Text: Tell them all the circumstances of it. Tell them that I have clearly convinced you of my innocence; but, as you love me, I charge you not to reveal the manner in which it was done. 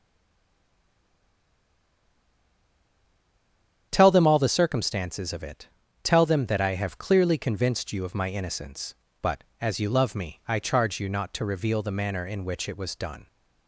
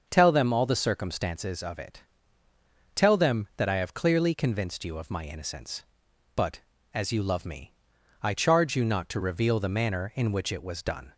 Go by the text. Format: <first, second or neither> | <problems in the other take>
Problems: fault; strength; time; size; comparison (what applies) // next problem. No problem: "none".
second | stays silent before the first word; strong; until 3.9 s; 3.9 s long // starts louder than the rest; strong; until 4.9 s; 9 dB; also in the second